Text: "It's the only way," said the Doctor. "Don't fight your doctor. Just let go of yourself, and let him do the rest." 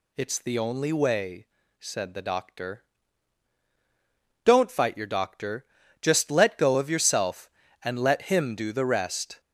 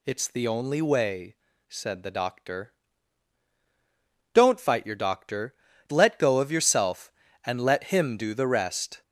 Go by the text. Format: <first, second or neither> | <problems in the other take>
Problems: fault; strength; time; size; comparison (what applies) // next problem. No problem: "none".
first | skips "Just"; at 5.7 s